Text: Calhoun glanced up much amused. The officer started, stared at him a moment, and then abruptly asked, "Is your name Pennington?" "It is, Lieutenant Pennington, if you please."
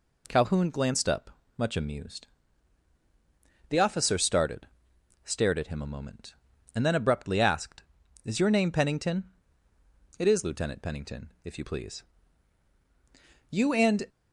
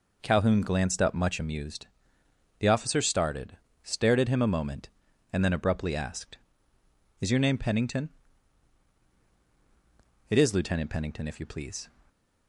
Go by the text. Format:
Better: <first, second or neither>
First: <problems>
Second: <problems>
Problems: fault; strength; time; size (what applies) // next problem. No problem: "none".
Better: second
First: pauses between "up" and "much"; slight; at 1.2 s; 0.28 s long // goes on to say "You and"; from 13.5 s on; 0.56 s long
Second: none